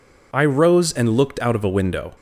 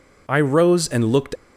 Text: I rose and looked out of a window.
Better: first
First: none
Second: stops before "out of a window"; at 1.3 s

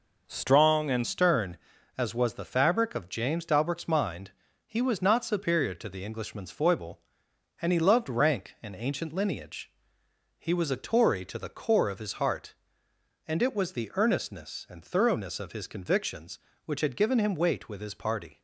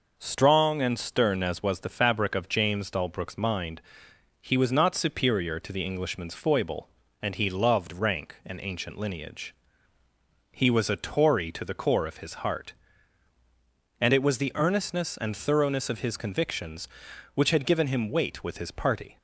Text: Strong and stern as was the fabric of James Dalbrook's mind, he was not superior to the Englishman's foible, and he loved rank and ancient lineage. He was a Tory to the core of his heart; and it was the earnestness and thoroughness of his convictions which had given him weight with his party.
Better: second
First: changes voice at "stern"; from 1.0 s on; 17.4 s long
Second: none

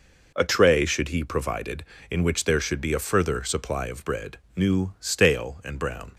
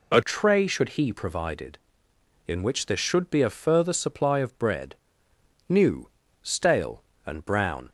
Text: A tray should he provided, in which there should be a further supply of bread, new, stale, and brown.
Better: first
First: none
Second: changes voice at "tray"; from 0.2 s on; 7.6 s long

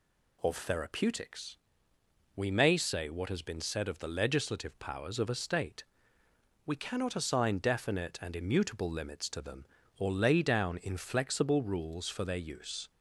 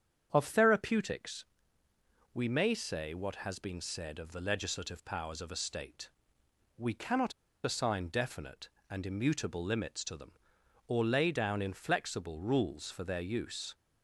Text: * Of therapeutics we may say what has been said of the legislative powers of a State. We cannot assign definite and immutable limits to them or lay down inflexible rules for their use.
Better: first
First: pauses between "therapeutics" and "we"; noticeable; at 1.5 s; 0.78 s long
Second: starts louder than the rest; strong; until 1.3 s; 8 dB // pauses between "therapeutics" and "we"; noticeable; at 1.4 s; 0.90 s long // pauses between "cannot" and "assign"; slight; at 7.3 s; 0.31 s long

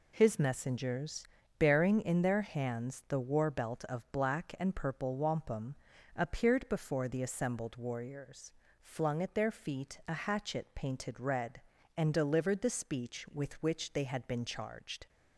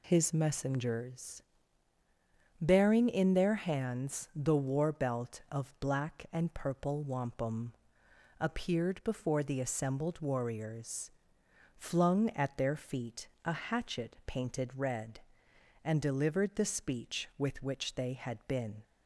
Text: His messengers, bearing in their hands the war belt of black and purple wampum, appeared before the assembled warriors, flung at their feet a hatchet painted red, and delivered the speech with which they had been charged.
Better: first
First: none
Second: pauses between "feet" and "a"; slight; at 13.2 s; 0.16 s long // stops before "charged"; at 18.8 s

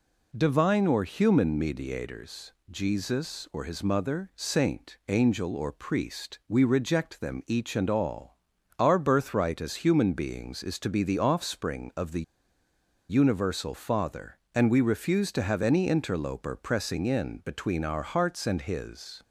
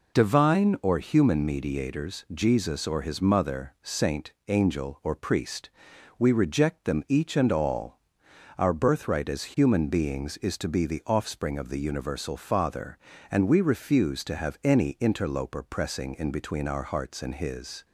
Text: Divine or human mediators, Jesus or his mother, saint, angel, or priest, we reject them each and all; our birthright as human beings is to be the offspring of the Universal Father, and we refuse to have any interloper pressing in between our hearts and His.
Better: second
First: pauses between "the" and "Universal"; noticeable; at 12.2 s; 0.87 s long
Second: none

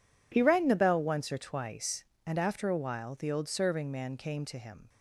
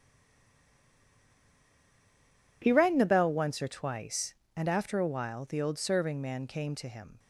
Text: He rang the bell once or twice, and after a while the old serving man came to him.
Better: first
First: none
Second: stays silent before the first word; strong; until 2.6 s; 2.6 s long

